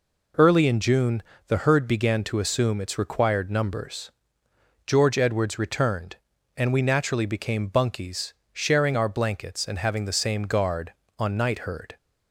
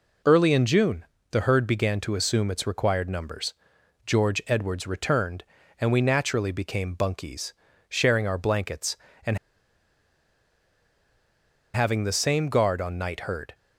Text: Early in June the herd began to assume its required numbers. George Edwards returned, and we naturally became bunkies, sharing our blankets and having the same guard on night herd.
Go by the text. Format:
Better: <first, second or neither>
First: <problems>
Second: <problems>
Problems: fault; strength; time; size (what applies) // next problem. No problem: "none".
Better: first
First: pauses between "June" and "the"; slight; at 1.2 s; 0.24 s long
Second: pauses between "June" and "the"; slight; at 1.0 s; 0.26 s long // pauses between "and" and "having"; strong; at 9.3 s; 2.3 s long